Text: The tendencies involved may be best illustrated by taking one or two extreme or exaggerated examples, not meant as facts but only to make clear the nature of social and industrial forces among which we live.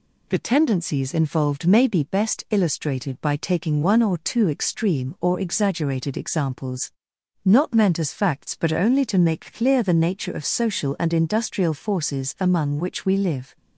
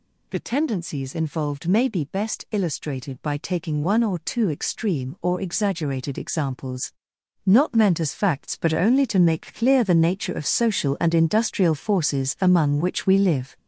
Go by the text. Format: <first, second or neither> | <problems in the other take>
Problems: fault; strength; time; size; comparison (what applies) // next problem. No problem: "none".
first | gets louder; throughout; 6.5 dB